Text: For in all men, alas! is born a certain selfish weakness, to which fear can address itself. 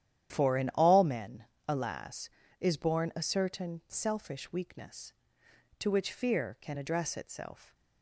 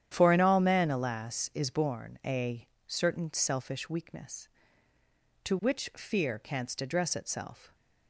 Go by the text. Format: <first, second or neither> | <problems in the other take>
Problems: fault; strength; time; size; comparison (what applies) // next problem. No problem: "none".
first | starts louder than the rest; strong; until 1.1 s; 10 dB; strong in the first // pauses between "a" and "certain"; slight; at 2.6 s; 0.20 s long // says "canst" for "can"; at 6.3 s